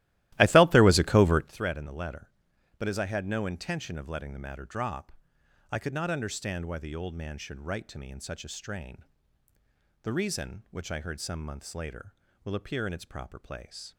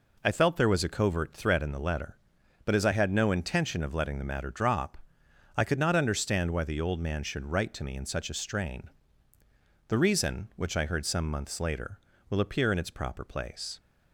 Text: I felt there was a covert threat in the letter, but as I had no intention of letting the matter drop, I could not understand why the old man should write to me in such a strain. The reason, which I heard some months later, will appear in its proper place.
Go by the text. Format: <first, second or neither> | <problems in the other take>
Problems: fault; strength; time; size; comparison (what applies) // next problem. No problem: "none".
second | starts louder than the rest; strong; until 1.5 s; 16 dB